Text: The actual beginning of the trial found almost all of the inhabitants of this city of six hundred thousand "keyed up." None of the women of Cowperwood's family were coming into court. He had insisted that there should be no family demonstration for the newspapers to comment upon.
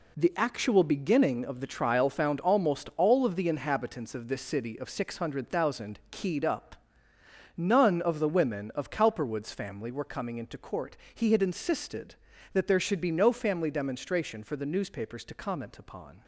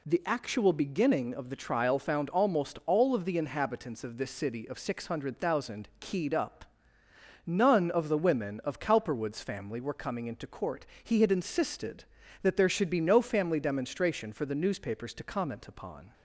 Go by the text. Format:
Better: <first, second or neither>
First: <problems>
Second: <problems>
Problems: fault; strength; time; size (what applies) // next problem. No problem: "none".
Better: second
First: gets quieter; strong; throughout; 9 dB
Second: none